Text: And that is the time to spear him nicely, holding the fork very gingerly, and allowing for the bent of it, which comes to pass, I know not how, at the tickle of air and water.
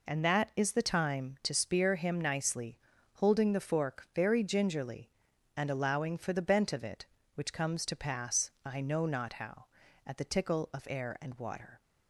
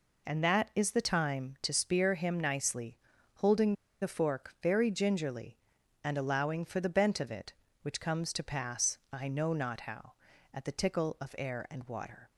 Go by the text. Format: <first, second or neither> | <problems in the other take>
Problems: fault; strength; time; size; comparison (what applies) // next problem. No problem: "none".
first | pauses between "holding" and "the"; slight; at 3.7 s; 0.27 s long